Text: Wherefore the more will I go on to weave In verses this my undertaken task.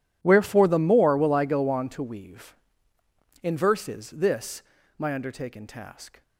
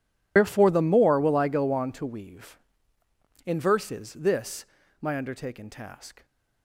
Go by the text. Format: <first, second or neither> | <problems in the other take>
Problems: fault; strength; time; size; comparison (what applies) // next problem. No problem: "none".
first | loses the start of "Wherefore"; at 0.3 s; 105 ms // pauses between "this" and "my"; slight; at 4.6 s; 0.36 s long; slight in the first